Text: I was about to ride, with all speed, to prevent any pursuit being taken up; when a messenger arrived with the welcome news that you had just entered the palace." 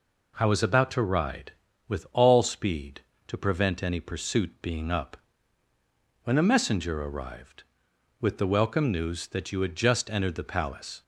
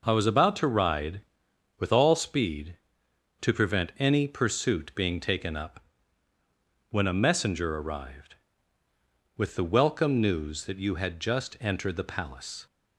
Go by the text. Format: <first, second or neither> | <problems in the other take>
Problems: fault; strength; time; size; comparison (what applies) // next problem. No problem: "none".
second | skips "taken"; at 4.9 s